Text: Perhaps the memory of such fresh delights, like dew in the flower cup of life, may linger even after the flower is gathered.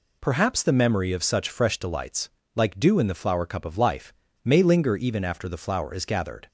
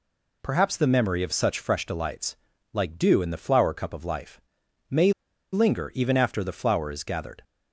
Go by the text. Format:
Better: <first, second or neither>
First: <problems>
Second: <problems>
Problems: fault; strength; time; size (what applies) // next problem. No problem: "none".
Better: first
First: none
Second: pauses between "may" and "linger"; at 5.1 s; 0.41 s long